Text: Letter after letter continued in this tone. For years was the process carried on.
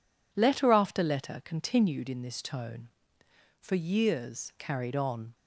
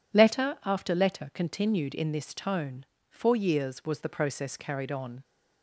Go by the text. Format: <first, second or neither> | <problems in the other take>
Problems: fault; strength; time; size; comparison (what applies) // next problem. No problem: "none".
second | skips "was the process"; at 4.5 s